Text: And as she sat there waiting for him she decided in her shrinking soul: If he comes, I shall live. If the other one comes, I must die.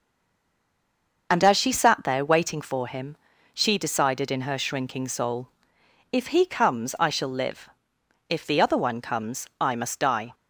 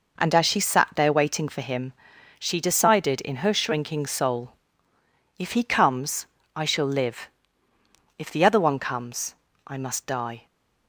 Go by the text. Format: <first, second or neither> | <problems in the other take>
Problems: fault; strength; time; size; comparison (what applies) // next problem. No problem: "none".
second | stays silent before the first word; noticeable; until 1.2 s; 1.2 s long // pauses between "him" and "she"; at 3.1 s; 0.40 s long; noticeable in the second